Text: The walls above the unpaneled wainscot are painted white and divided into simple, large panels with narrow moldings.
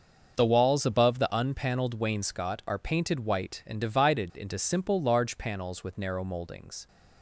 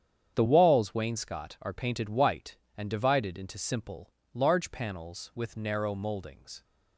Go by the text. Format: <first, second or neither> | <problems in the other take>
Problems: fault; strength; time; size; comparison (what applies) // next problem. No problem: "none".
first | starts louder than the rest; strong; until 1.3 s; 8.5 dB; also in the first // skips "above the unpaneled"; at 0.9 s